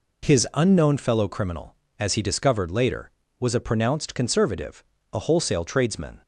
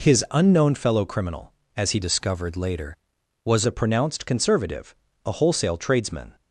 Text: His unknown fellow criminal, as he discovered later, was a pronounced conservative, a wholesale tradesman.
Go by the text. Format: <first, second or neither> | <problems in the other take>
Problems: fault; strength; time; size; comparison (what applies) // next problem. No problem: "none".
first | changes voice from "discovered" to "was"; from 2.0 to 3.6 s; 1.6 s long